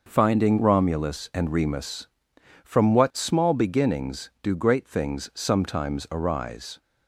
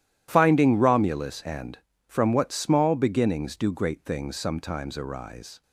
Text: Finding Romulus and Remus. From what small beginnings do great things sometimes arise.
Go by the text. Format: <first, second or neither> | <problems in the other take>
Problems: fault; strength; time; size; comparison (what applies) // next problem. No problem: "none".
first | starts louder than the rest; strong; until 1.3 s; 12 dB // skips "Remus"; at 1.9 s